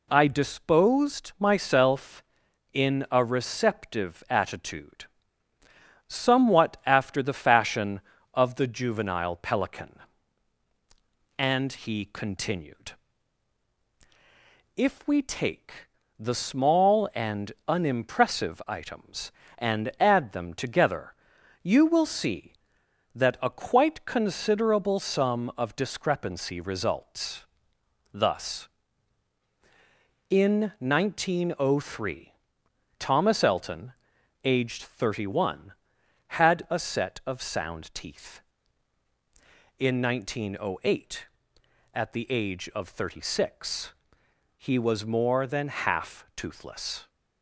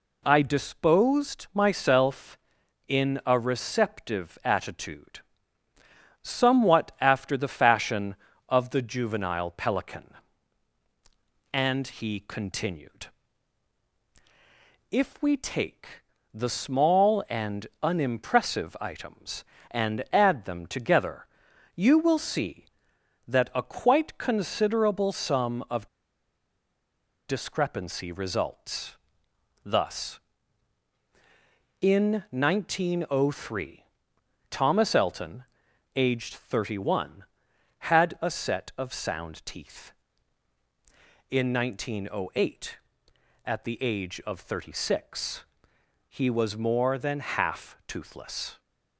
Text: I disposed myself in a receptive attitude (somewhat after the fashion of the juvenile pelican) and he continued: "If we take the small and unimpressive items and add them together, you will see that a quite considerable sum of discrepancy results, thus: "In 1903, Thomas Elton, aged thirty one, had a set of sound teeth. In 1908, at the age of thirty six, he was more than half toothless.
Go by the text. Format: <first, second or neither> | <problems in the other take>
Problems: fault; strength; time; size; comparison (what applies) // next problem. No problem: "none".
first | pauses between "take" and "the"; slight; at 16.0 s; 0.30 s long; slight in the first // pauses between "and" and "unimpressive"; slight; at 17.6 s; 0.16 s long; slight in the first // pauses between "of" and "discrepancy"; strong; at 25.8 s; 1.3 s long